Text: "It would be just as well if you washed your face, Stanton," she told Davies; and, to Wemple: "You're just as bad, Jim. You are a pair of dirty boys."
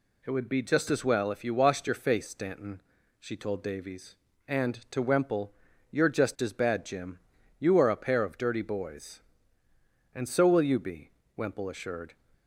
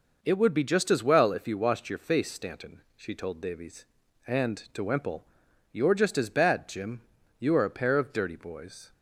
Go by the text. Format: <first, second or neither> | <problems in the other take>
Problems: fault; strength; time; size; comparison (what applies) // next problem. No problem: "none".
second | goes on to say "And so will you be Wemple assured"; strong; from 10.1 s on; 2.0 s long